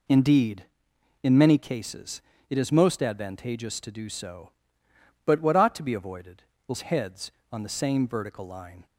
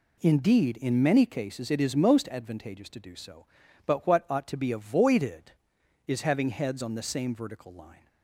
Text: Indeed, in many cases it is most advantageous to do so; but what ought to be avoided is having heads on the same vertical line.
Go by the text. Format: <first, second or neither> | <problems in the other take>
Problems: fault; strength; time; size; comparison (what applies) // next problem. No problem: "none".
second | pauses between "cases" and "it"; slight; at 2.2 s; 0.28 s long // skips "having"; at 6.8 s